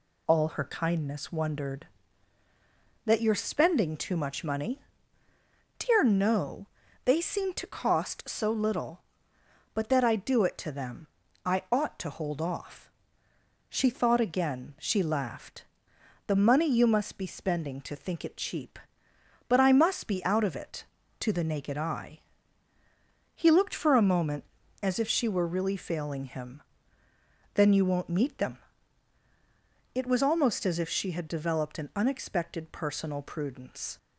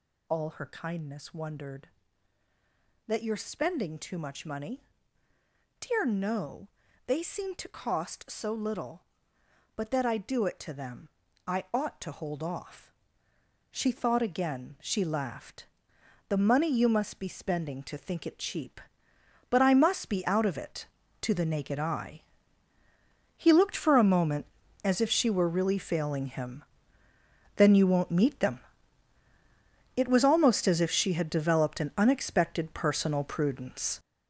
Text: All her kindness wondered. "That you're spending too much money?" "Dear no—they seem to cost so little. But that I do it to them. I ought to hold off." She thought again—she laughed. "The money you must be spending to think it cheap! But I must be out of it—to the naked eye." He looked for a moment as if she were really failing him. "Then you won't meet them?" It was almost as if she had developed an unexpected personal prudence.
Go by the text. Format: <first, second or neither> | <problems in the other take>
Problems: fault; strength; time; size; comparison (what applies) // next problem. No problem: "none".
first | gets louder; strong; throughout; 8.5 dB